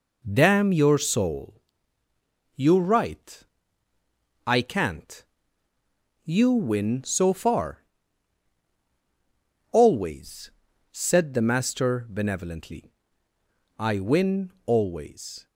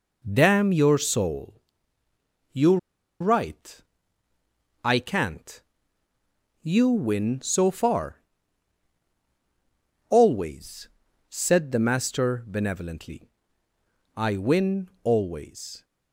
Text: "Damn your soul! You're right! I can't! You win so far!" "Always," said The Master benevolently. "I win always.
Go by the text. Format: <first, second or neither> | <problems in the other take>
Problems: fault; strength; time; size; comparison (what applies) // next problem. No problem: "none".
first | pauses between "You're" and "right"; at 2.7 s; 0.43 s long // pauses between "win" and "always"; slight; at 14.8 s; 0.16 s long; slight in the first